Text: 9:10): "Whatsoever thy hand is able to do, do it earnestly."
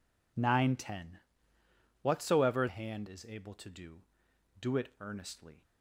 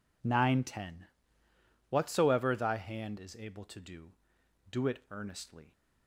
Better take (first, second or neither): second